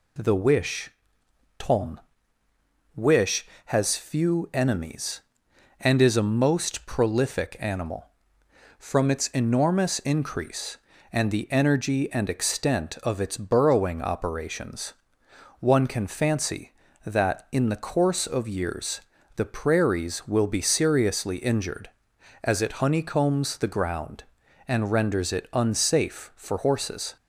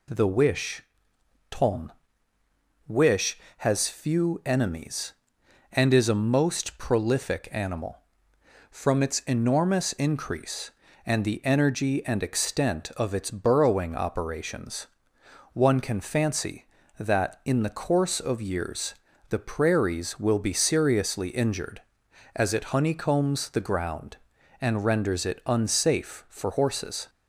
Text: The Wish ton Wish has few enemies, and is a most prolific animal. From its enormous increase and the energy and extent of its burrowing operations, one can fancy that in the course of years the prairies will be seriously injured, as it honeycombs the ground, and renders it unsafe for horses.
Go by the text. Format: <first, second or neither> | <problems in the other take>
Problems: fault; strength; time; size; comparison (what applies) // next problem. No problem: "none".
neither | pauses between "Wish" and "ton"; noticeable; the same in both // pauses between "ton" and "Wish"; noticeable; the same in both // pauses between "years" and "the"; slight; the same in both